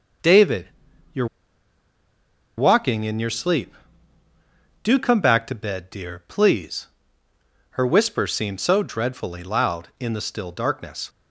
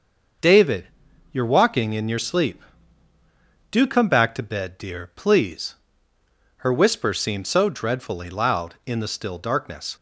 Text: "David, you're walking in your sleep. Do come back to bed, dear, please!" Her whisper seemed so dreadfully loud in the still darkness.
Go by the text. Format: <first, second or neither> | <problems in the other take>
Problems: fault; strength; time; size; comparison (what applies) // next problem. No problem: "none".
second | starts louder than the rest; noticeable; until 3.0 s; 6 dB; noticeable in the second // pauses between "you're" and "walking"; strong; at 1.2 s; 1.3 s long